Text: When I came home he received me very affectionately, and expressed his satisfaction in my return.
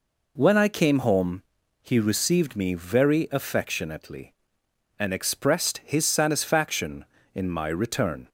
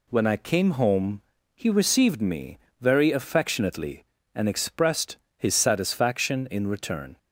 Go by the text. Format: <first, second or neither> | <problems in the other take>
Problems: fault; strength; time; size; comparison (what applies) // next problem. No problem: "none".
first | pauses between "home" and "he"; slight; at 1.1 s; 0.34 s long; also in the first // pauses between "me" and "very"; slight; at 2.5 s; 0.22 s long // pauses between "expressed" and "his"; slight; at 5.1 s; 0.18 s long // skips "my"; at 6.6 s